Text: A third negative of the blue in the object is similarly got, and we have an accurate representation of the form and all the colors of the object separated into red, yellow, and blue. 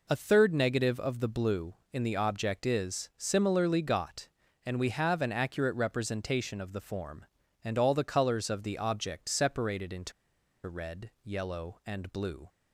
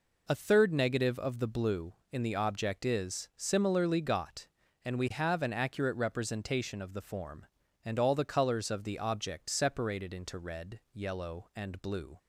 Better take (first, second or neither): second